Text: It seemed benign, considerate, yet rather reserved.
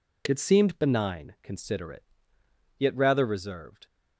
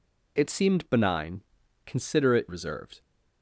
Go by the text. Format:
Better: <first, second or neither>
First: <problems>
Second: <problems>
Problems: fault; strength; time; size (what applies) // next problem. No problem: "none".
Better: first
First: none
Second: skips "yet rather"; at 2.4 s